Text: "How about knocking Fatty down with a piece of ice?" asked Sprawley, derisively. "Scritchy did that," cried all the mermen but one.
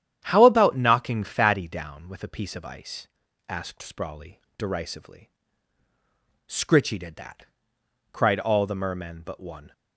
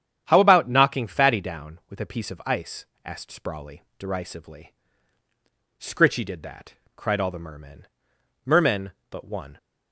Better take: first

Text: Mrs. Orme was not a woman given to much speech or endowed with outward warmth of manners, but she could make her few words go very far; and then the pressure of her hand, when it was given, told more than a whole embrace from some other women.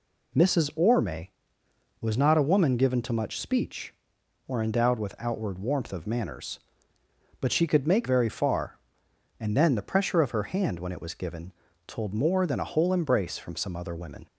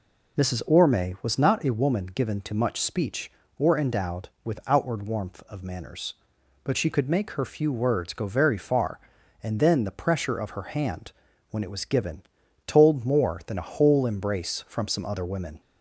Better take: second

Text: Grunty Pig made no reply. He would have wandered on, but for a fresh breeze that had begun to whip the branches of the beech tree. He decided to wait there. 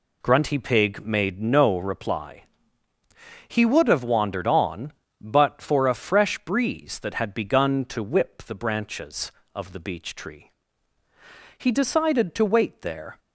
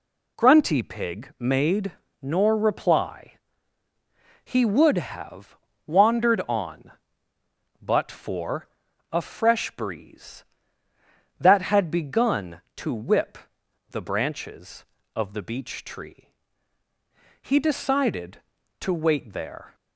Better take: first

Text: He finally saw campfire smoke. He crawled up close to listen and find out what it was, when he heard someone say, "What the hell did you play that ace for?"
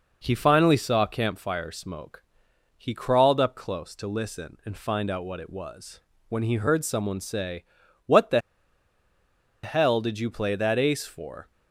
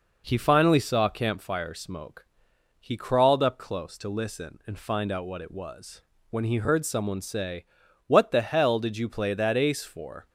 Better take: second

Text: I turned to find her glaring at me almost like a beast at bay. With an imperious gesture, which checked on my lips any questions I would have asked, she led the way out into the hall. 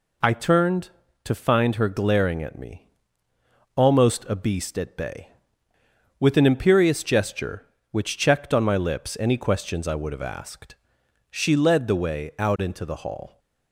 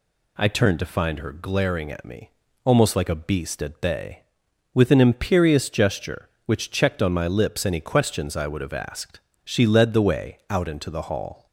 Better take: second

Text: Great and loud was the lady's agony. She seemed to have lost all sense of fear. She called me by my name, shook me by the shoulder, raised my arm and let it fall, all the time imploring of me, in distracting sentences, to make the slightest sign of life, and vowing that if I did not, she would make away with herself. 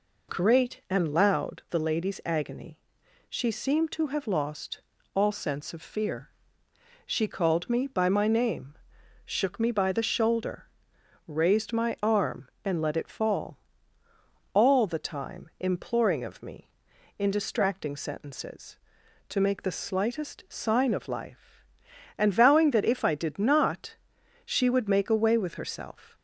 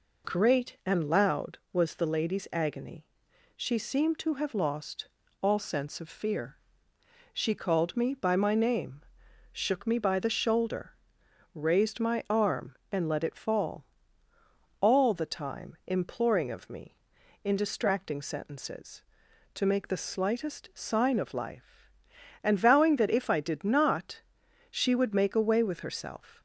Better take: second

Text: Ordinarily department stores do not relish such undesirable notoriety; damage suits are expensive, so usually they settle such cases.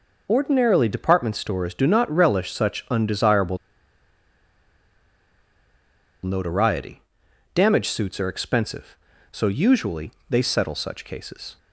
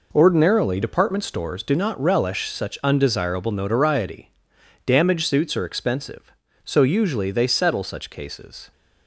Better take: second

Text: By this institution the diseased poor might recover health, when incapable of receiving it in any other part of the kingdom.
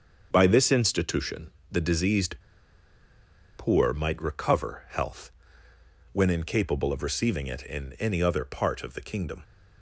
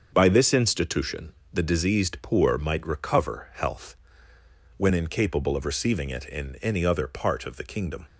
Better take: second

